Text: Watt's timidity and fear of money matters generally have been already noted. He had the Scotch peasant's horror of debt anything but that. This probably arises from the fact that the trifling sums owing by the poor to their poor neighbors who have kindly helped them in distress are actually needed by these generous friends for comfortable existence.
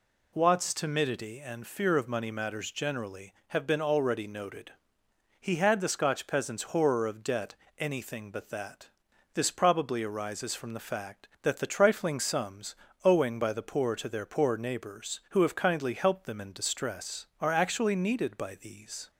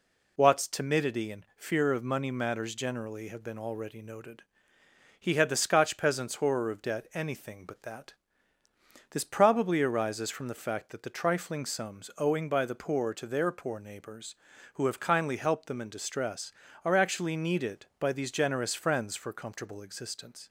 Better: second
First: pauses between "debt" and "anything"; slight; at 7.5 s; 0.24 s long // pauses between "sums" and "owing"; slight; at 12.7 s; 0.30 s long // stops before "generous friends for comfortable existence"; at 19.1 s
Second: none

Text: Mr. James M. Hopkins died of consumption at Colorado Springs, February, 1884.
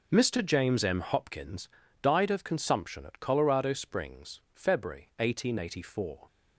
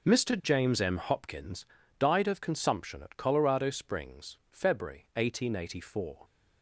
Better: neither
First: pauses between "Hopkins" and "died"; slight; at 1.6 s; 0.36 s long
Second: pauses between "Hopkins" and "died"; slight; at 1.6 s; 0.36 s long

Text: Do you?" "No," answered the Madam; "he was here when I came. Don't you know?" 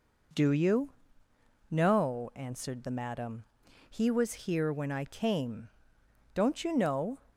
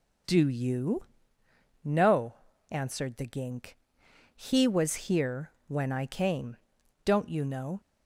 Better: first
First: none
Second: says "Gink" for "Madam"; at 3.2 s // pauses between "here" and "when"; slight; at 5.5 s; 0.16 s long

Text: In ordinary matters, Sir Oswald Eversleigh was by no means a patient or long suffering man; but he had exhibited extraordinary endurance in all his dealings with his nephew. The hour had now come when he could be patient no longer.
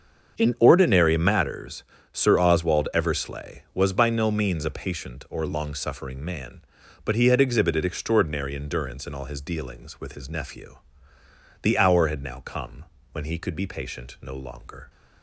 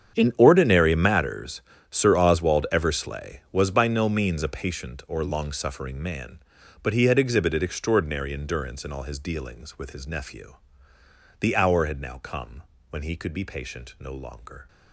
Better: first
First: starts louder than the rest; until 1.4 s; 7 dB // pauses between "come" and "when"; slight; at 12.8 s; 0.30 s long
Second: gets quieter; strong; throughout; 16.5 dB // starts louder than the rest; strong; until 1.2 s; 8.5 dB // pauses between "come" and "when"; slight; at 12.6 s; 0.30 s long

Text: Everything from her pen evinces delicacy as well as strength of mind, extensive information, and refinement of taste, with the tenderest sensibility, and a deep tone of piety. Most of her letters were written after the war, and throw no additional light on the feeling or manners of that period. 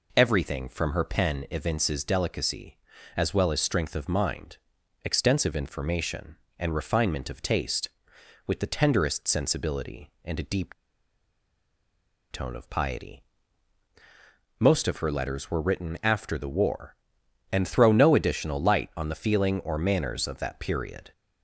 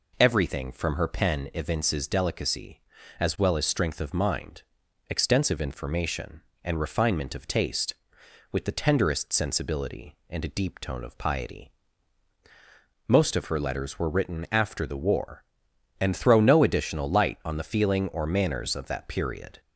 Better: second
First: pauses between "deep" and "tone"; strong; at 10.7 s; 1.5 s long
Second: none

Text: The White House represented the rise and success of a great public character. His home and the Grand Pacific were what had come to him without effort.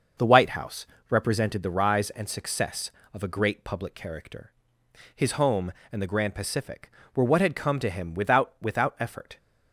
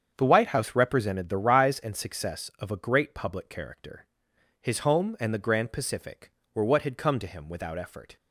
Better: second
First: starts louder than the rest; noticeable; until 1.4 s; 6 dB // pauses between "House" and "represented"; slight; at 0.8 s; 0.24 s long // says "without" twice; at 8.6 s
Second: starts louder than the rest; strong; until 1.1 s; 7.5 dB

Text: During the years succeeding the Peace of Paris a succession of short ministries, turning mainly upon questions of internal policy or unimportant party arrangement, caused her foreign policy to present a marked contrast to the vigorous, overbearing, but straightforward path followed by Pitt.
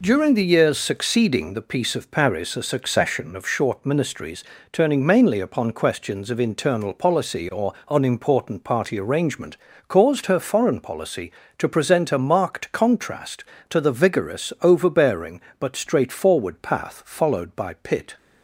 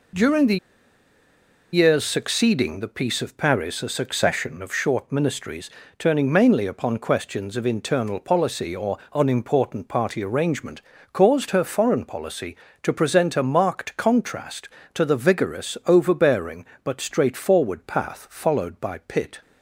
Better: first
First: pauses between "or" and "unimportant"; slight; at 7.7 s; 0.16 s long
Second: pauses between "the" and "years"; at 0.5 s; 1.1 s long // pauses between "or" and "unimportant"; slight; at 8.9 s; 0.16 s long

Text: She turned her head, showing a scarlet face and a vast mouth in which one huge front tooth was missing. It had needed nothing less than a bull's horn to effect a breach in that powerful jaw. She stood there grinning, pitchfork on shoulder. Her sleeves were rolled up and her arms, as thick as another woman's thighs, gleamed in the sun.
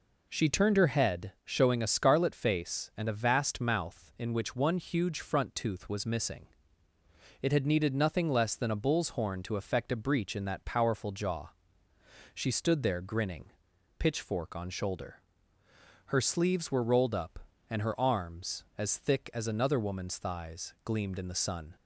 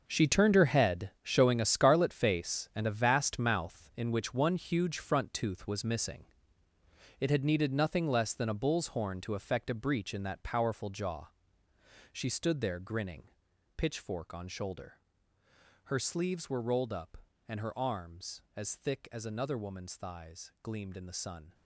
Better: first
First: none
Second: gets quieter; strong; throughout; 12.5 dB

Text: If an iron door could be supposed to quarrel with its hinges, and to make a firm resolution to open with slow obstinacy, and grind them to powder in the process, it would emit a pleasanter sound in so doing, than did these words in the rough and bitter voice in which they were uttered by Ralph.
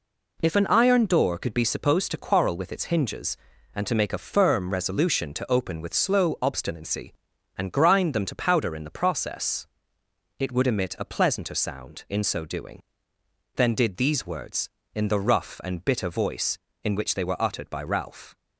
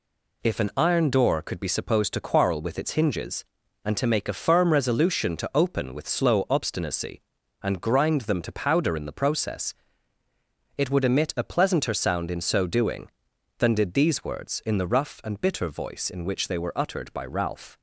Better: neither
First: none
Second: none

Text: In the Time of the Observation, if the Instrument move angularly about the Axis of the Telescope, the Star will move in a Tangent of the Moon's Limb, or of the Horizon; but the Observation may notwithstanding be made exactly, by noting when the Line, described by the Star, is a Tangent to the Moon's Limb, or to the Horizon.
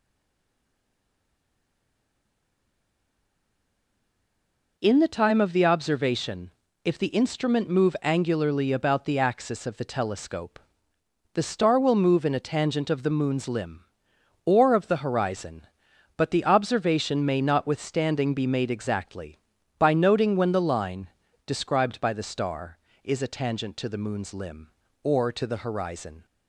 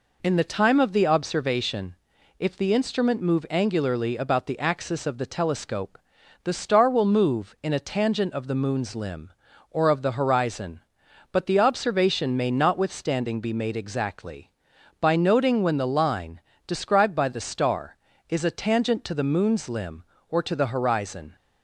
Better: second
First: stays silent before the first word; strong; until 4.7 s; 4.7 s long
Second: none

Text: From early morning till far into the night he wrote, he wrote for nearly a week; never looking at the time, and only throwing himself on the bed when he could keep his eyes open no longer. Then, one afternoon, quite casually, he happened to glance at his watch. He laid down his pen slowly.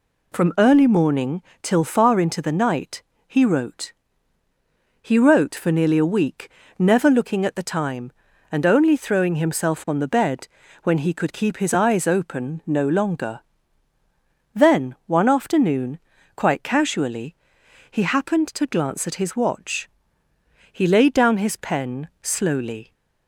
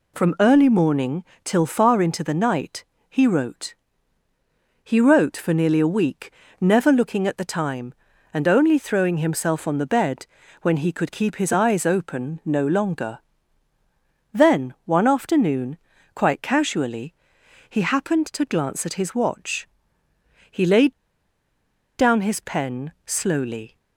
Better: first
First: pauses between "morning" and "till"; slight; at 1.4 s; 0.18 s long // pauses between "night" and "he"; slight; at 3.0 s; 0.26 s long // pauses between "bed" and "when"; at 10.4 s; 0.38 s long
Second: pauses between "morning" and "till"; slight; at 1.2 s; 0.18 s long // pauses between "night" and "he"; slight; at 2.8 s; 0.26 s long // pauses between "bed" and "when"; at 10.2 s; 0.38 s long // pauses between "laid" and "down"; at 20.9 s; 1.0 s long

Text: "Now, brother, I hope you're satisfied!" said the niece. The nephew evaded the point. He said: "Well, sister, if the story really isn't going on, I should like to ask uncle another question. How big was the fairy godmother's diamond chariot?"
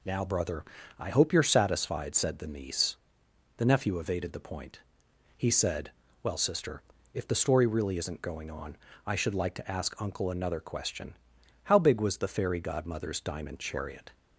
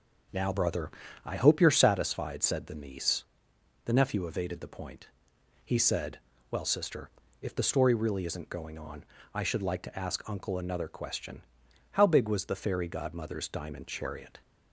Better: first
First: none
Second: starts louder than the rest; noticeable; until 1.9 s; 5.5 dB

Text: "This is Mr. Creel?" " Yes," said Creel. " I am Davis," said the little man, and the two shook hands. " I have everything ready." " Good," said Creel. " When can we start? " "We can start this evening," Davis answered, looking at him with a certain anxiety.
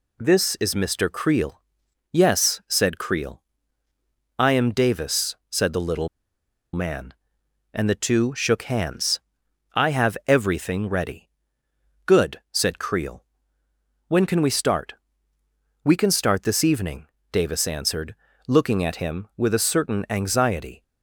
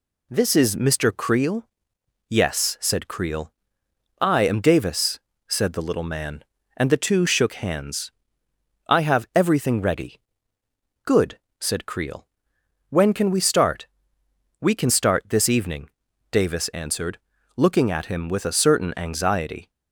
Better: second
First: pauses between "little" and "man"; noticeable; at 6.0 s; 0.65 s long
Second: none

